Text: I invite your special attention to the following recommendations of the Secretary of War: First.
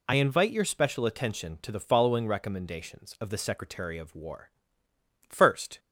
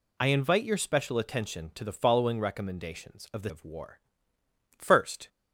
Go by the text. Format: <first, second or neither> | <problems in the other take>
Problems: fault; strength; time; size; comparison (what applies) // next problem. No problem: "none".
first | skips "Secretary"; at 3.4 s